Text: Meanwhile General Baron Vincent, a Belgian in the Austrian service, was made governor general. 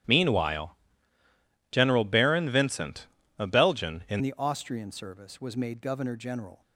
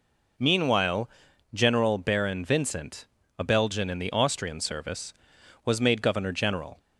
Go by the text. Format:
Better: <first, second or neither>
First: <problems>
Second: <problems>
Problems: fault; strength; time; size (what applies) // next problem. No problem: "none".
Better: second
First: starts louder than the rest; strong; until 2.0 s; 11.5 dB // pauses between "Meanwhile" and "General"; noticeable; at 0.7 s; 0.96 s long // changes voice at "the"; from 4.2 s on; 2.4 s long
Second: pauses between "Meanwhile" and "General"; at 1.0 s; 0.44 s long